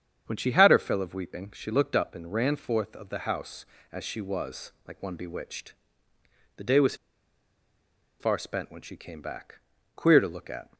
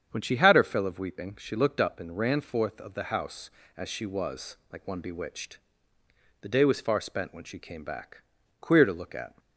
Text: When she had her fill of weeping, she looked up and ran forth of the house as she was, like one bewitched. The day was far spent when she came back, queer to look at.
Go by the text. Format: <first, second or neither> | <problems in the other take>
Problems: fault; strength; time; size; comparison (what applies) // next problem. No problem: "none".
second | starts louder than the rest; strong; until 1.2 s; 8 dB; strong in the second // pauses between "was" and "far"; at 6.9 s; 1.2 s long